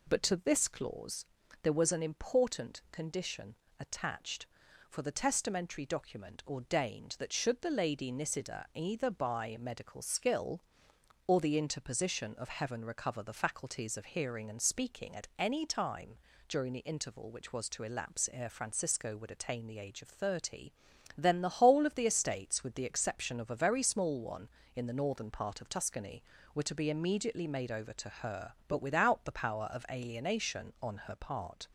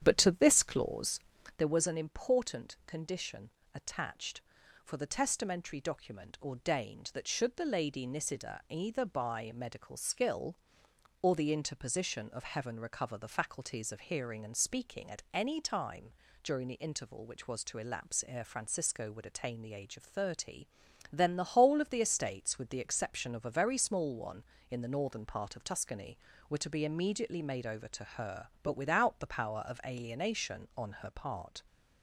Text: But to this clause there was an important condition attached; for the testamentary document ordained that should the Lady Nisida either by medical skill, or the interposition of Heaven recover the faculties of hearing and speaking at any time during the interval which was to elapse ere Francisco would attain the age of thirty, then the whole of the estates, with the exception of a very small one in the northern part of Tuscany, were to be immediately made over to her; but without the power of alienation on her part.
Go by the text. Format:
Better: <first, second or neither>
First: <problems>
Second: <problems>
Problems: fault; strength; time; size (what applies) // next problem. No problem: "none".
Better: first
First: pauses between "clause" and "there"; slight; at 1.2 s; 0.36 s long // pauses between "condition" and "attached"; slight; at 3.5 s; 0.22 s long // pauses between "time" and "during"; slight; at 16.1 s; 0.32 s long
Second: starts louder than the rest; strong; until 1.6 s; 9.5 dB // pauses between "clause" and "there"; slight; at 1.2 s; 0.36 s long // pauses between "condition" and "attached"; slight; at 3.5 s; 0.22 s long // pauses between "time" and "during"; slight; at 16.1 s; 0.32 s long